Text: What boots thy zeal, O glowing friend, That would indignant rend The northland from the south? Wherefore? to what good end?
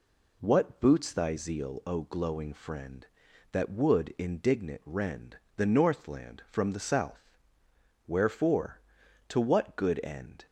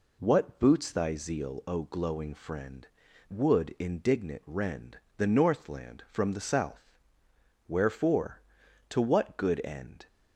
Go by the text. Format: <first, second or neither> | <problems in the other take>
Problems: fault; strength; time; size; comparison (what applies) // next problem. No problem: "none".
first | skips "That"; at 3.1 s // pauses between "rend" and "The"; slight; at 4.9 s; 0.18 s long; slight in the first